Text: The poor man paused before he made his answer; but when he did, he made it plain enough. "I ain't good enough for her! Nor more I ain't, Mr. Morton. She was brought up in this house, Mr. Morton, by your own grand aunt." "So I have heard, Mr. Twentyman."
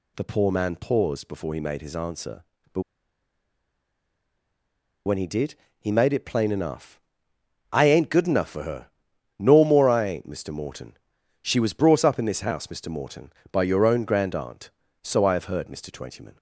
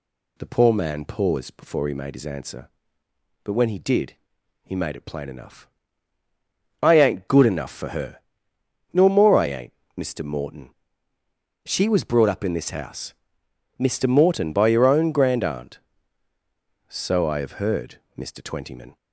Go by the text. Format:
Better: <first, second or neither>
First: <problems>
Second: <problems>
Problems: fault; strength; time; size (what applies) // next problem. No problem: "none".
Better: second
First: pauses between "but" and "when"; strong; at 2.8 s; 2.2 s long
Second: none